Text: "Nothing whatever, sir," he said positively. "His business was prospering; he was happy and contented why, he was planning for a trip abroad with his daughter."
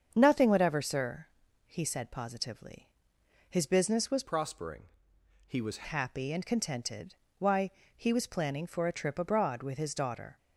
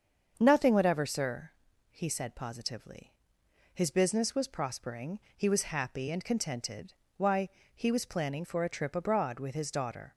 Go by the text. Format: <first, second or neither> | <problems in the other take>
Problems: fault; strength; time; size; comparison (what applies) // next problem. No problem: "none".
second | starts louder than the rest; strong; until 1.1 s; 7.5 dB; strong in the second // changes voice from "prospering" to "was"; from 4.2 to 5.8 s; 1.6 s long // pauses between "contented" and "why"; slight; at 7.1 s; 0.26 s long; slight in the second